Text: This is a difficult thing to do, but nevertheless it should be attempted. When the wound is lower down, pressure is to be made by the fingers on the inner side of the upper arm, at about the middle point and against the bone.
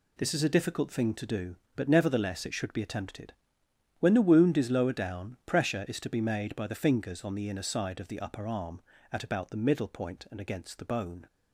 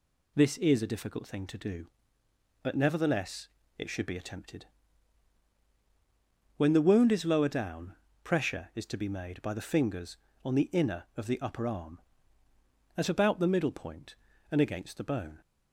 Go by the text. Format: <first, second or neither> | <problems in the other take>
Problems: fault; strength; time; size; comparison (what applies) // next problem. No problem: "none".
first | pauses between "nevertheless" and "it"; slight; at 3.4 s; 0.30 s long // skips "side"; at 11.0 s